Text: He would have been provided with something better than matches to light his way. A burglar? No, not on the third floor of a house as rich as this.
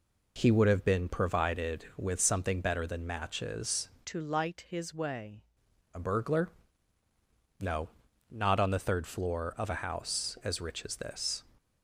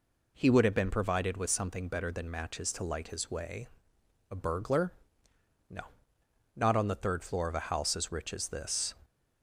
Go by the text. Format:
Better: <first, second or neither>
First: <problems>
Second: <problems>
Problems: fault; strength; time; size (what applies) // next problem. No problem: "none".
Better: second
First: changes voice from "to" to "way"; from 4.0 to 5.4 s; 1.4 s long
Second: none